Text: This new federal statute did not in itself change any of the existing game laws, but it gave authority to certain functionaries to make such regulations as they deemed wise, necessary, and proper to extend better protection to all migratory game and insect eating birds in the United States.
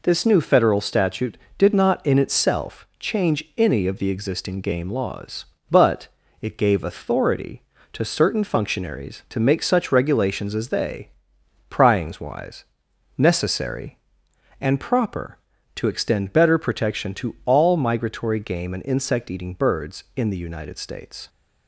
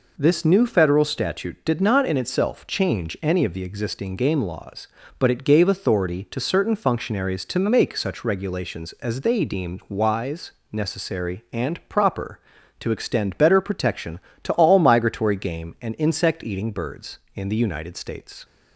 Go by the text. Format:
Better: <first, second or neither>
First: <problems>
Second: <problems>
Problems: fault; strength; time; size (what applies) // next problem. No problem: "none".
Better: second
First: pauses between "but" and "it"; slight; at 6.0 s; 0.34 s long // says "pryings" for "deemed"; at 11.6 s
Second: none